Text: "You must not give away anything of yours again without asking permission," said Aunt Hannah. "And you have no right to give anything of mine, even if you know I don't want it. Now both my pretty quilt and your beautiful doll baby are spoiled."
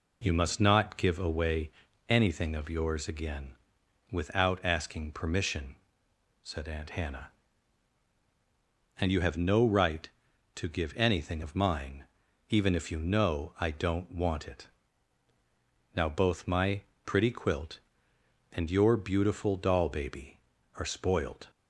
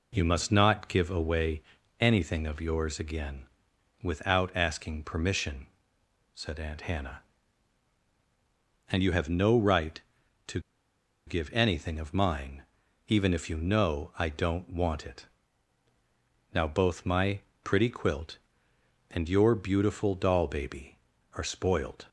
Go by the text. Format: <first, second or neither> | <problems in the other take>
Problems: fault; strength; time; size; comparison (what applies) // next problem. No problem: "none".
first | pauses between "away" and "anything"; slight; at 1.6 s; 0.36 s long; slight in the first // pauses between "again" and "without"; noticeable; at 3.4 s; 0.52 s long; noticeable in the first // pauses between "to" and "give"; noticeable; at 10.5 s; 0.67 s long // pauses between "my" and "pretty"; slight; at 17.4 s; 0.24 s long; slight in the first